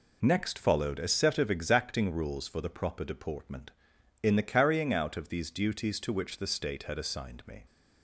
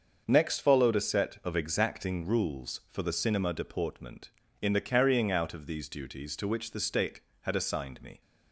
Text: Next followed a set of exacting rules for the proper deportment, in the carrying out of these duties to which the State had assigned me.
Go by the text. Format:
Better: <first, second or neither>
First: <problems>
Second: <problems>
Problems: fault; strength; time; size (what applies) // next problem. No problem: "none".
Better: first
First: none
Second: starts louder than the rest; until 1.2 s; 6.5 dB // says "cinema" for "proper"; at 3.1 s